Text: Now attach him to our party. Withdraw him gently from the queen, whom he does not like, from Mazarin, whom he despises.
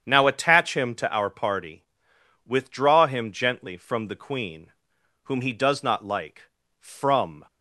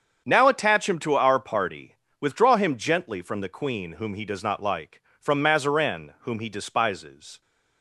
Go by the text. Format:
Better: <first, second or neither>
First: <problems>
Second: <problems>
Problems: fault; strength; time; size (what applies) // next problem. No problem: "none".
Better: second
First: starts louder than the rest; strong; until 1.0 s; 8 dB // stops before "Mazarin whom he despises"; at 7.4 s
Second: starts louder than the rest; strong; until 1.2 s; 7.5 dB